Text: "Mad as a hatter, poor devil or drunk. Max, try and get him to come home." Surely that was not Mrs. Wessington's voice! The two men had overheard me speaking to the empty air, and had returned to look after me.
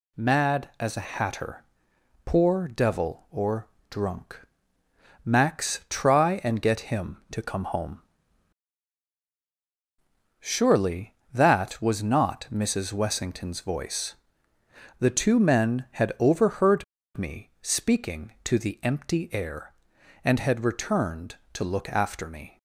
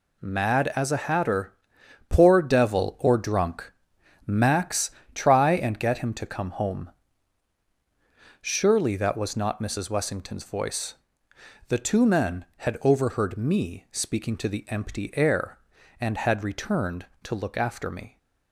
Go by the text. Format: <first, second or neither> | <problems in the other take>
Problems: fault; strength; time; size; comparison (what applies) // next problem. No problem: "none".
second | pauses between "or" and "drunk"; slight; at 3.6 s; 0.22 s long // pauses between "overheard" and "me"; slight; at 16.8 s; 0.32 s long